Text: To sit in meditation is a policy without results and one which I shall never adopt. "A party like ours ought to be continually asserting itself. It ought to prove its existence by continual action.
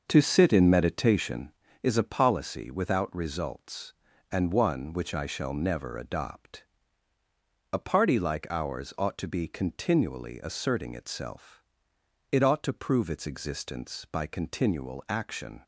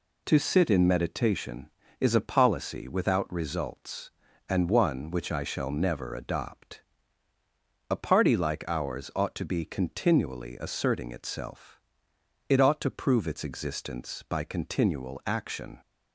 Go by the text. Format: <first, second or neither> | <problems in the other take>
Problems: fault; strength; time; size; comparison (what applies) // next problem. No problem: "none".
second | starts louder than the rest; noticeable; until 1.6 s; 6 dB